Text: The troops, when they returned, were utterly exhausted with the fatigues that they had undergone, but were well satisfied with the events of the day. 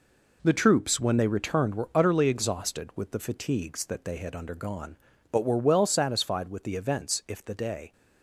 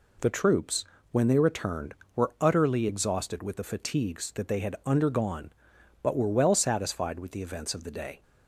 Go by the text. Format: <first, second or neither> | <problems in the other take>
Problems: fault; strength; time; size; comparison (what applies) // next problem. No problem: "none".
second | says "if" for "of"; at 7.2 s